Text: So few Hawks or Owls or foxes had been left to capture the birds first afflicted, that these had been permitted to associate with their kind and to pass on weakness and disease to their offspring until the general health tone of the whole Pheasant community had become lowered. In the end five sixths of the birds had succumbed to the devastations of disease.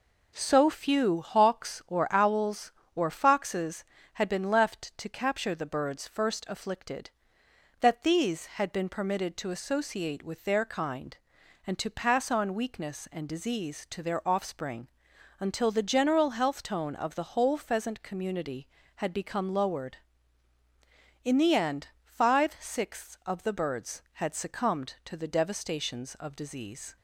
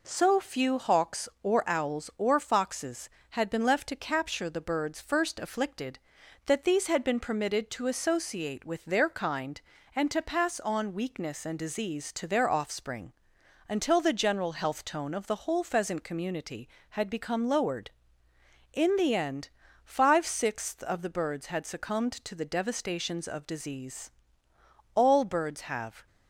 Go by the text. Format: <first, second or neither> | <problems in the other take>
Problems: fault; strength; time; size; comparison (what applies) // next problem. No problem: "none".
first | pauses between "offspring" and "until"; noticeable; at 13.1 s; 0.54 s long; noticeable in the first // pauses between "end" and "five"; slight; at 19.4 s; 0.34 s long; slight in the first // goes on to say "All birds have"; noticeable; from 24.9 s on; 1.1 s long